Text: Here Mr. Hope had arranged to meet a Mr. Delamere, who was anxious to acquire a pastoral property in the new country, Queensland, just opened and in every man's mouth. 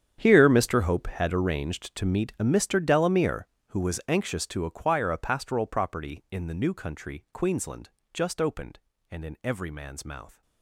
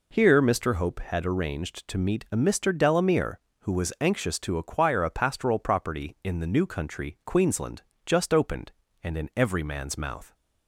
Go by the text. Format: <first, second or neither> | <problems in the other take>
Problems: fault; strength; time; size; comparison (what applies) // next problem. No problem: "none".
second | gets quieter; strong; throughout; 16 dB